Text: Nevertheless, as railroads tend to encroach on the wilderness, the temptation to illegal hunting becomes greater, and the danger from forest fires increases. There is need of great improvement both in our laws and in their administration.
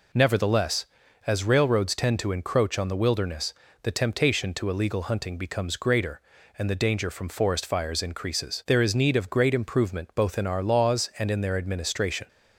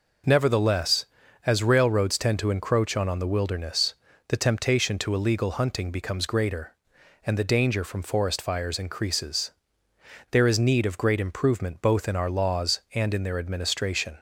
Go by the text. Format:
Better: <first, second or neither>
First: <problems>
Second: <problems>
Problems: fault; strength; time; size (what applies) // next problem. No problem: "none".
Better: first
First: none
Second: says "on" twice; at 3.0 s